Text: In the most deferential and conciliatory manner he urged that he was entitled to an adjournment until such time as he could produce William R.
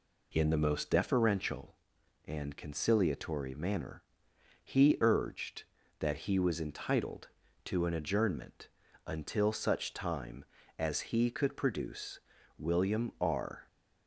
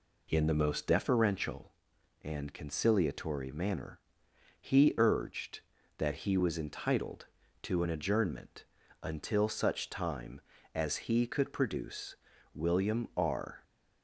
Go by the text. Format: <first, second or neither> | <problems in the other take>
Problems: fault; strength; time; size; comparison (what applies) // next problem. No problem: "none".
neither | pauses between "manner" and "he"; noticeable; the same in both // pauses between "adjournment" and "until"; slight; the same in both // pauses between "produce" and "William"; slight; the same in both